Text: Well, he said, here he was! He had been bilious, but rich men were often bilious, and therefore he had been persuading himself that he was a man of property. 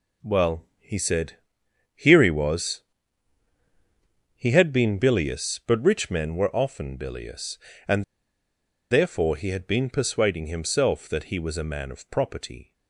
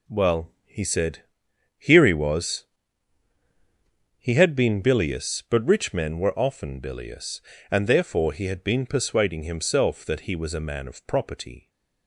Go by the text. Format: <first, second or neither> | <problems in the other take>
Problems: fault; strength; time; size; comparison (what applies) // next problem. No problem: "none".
second | pauses between "and" and "therefore"; noticeable; at 8.0 s; 0.86 s long